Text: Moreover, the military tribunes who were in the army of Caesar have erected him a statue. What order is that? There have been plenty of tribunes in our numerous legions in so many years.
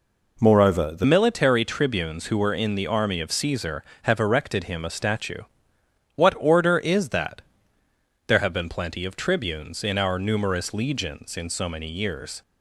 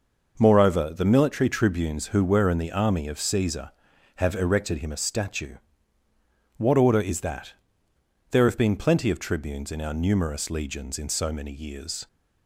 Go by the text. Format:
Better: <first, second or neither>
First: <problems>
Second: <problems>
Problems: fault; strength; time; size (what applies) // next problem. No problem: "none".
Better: second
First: changes voice at "military"; from 1.0 s on; 11.4 s long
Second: none